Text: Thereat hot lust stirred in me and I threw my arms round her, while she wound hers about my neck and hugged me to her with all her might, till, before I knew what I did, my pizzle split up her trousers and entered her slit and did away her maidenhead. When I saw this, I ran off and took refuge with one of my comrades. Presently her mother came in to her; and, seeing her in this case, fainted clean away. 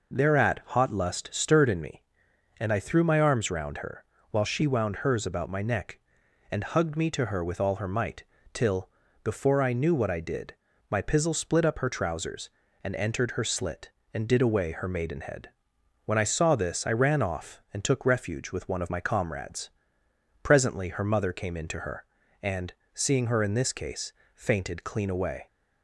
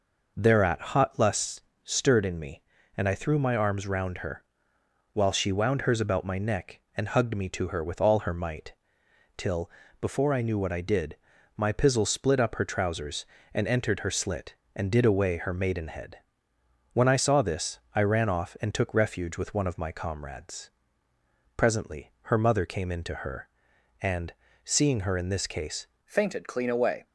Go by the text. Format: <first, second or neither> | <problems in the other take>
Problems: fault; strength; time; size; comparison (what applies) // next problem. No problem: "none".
first | pauses between "lust" and "stirred"; slight; at 1.6 s; 0.22 s long // changes voice at "fainted"; from 26.0 s on; 1.0 s long